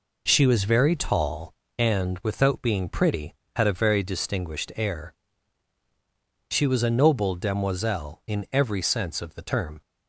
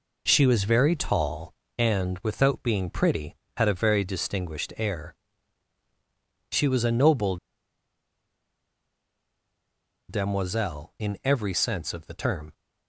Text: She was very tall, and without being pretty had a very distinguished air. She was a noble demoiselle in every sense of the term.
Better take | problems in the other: first | pauses between "noble" and "demoiselle"; strong; at 7.3 s; 2.7 s long

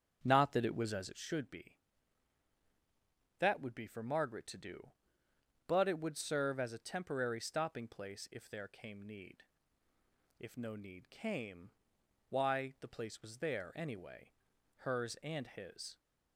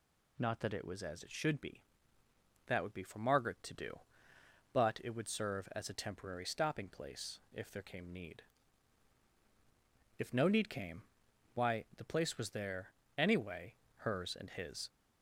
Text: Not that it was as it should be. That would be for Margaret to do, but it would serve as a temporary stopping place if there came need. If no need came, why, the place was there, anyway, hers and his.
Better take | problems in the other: second | starts louder than the rest; strong; until 1.4 s; 7.5 dB

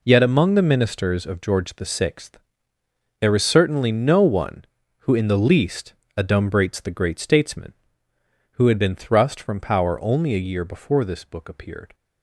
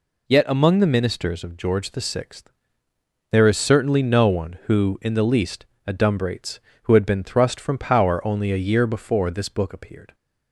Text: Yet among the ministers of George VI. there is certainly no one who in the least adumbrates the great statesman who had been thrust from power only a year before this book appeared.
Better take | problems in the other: first | pauses between "least" and "adumbrates"; slight; at 5.6 s; 0.20 s long; slight in the first // skips "the great statesman"; at 6.7 s

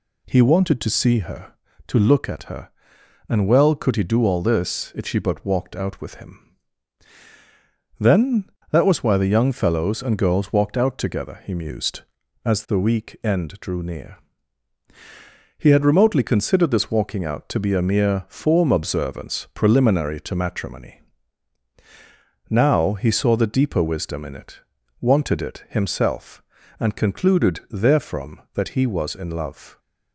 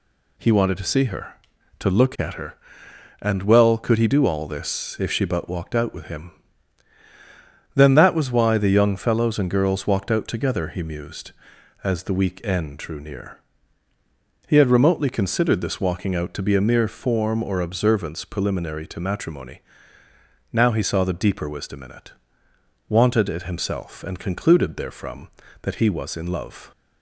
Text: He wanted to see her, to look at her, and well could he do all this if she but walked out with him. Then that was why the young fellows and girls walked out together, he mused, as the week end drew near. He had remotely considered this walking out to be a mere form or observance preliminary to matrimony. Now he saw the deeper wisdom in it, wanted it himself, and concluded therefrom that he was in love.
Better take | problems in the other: second | skips "or"; at 18.7 s

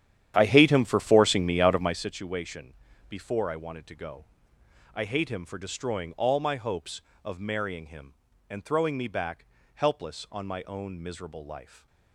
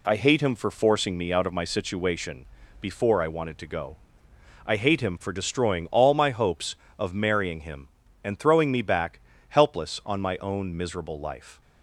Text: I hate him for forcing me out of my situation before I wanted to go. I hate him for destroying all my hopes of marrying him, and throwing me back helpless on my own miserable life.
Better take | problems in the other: second | starts louder than the rest; strong; until 2.0 s; 10.5 dB // pauses between "situation" and "before"; slight; at 2.7 s; 0.34 s long; slight in the second // pauses between "back" and "helpless"; slight; at 9.4 s; 0.28 s long; slight in the second

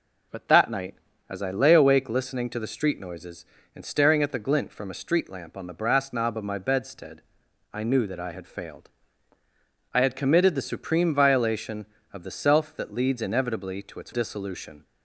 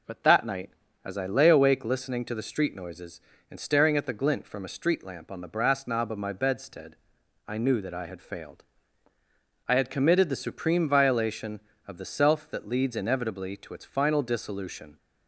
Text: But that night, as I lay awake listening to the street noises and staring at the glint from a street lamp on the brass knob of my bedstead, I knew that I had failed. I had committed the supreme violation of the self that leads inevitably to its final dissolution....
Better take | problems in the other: second | skips "final"; at 14.1 s

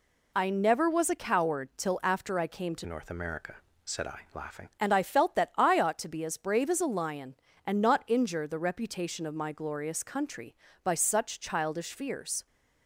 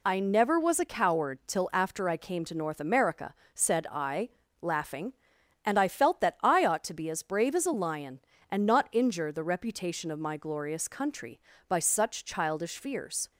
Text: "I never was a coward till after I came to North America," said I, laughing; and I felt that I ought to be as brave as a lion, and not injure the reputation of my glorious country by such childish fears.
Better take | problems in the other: second | changes voice from "North" to "laughing"; from 2.8 to 4.7 s; 1.9 s long

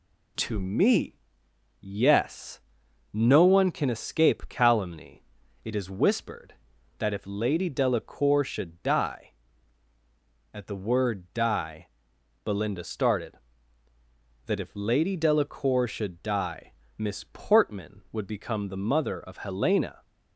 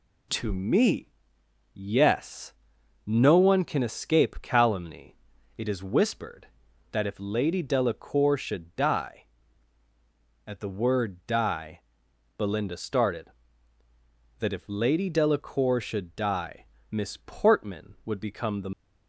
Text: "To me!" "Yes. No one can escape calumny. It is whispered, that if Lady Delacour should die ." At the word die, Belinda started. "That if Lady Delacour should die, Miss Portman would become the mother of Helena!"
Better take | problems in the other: first | stops before "mother of Helena"; at 18.7 s

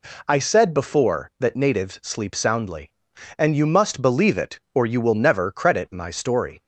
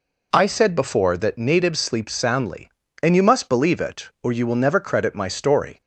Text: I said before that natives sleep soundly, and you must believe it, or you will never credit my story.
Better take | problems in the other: neither | none

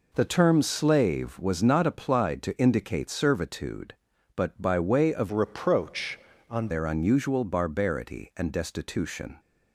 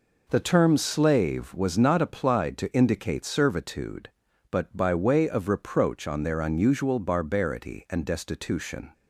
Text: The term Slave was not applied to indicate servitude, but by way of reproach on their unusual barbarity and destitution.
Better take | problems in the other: second | changes voice from "reproach" to "on"; from 5.3 to 6.6 s; 1.3 s long

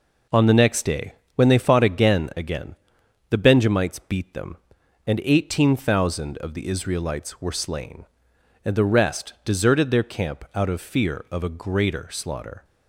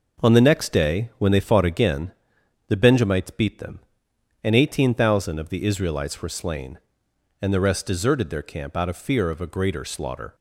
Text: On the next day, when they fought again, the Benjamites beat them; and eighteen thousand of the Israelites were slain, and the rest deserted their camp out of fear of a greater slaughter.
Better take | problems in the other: second | says "again" twice; at 2.3 s

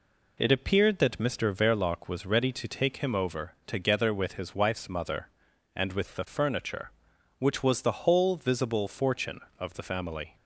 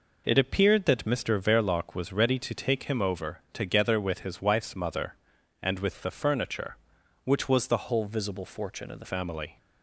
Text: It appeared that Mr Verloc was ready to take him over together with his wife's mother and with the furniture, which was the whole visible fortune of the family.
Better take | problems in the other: first | changes voice from "whole" to "the"; from 7.8 to 9.0 s; 1.2 s long

